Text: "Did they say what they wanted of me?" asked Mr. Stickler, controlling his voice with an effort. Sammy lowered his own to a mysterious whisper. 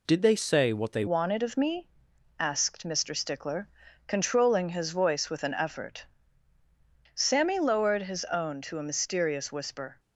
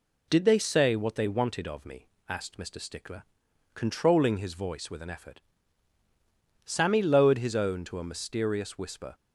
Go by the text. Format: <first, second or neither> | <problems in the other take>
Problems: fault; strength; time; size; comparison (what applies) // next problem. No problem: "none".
second | changes voice at "wanted"; from 1.0 s on; 8.9 s long